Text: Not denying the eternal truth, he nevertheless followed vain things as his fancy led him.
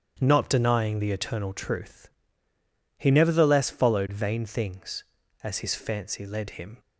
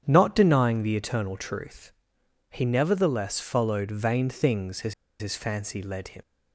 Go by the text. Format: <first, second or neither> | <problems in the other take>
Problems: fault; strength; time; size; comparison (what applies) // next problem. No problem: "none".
first | starts louder than the rest; strong; until 1.0 s; 8.5 dB; strong in the first // pauses between "as" and "his"; slight; at 4.9 s; 0.27 s long